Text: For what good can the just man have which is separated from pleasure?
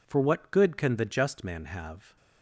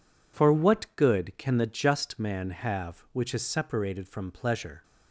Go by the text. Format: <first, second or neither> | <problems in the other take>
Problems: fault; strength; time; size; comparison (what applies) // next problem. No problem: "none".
second | stops before "which is separated from pleasure"; at 2.1 s